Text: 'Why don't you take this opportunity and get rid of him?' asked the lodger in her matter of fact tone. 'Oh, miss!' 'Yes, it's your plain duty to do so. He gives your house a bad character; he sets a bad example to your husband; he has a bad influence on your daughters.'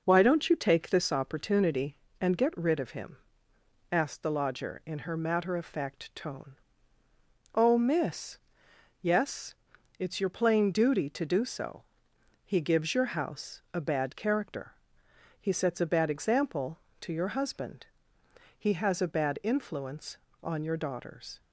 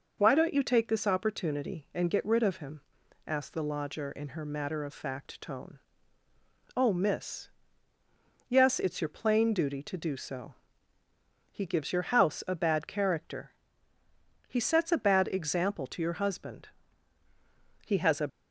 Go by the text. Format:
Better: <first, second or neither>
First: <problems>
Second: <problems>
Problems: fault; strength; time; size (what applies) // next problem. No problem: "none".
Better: first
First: none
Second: stops before "bad influence on your daughters"; at 18.2 s